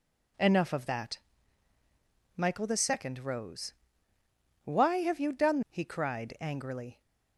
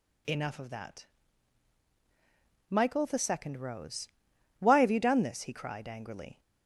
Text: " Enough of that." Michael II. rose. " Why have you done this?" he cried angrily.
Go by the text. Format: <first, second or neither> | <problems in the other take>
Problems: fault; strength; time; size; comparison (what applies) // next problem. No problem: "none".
second | skips "this"; at 5.6 s